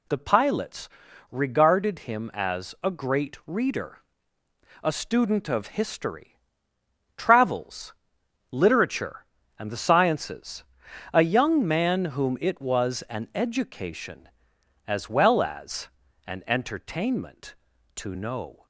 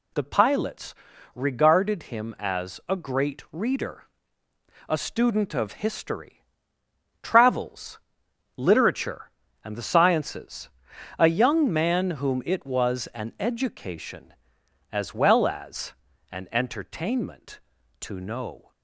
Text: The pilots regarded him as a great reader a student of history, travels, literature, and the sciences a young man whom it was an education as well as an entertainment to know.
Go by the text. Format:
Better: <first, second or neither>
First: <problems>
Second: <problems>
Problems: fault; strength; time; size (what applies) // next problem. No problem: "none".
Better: neither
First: pauses between "pilots" and "regarded"; at 0.8 s; 0.42 s long // pauses between "reader" and "a"; noticeable; at 3.9 s; 0.86 s long // pauses between "sciences" and "a"; noticeable; at 10.6 s; 0.48 s long // pauses between "as" and "an"; at 15.8 s; 0.38 s long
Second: pauses between "pilots" and "regarded"; at 0.9 s; 0.40 s long // pauses between "reader" and "a"; noticeable; at 4.0 s; 0.86 s long // pauses between "sciences" and "a"; noticeable; at 10.6 s; 0.48 s long // pauses between "as" and "an"; at 15.9 s; 0.38 s long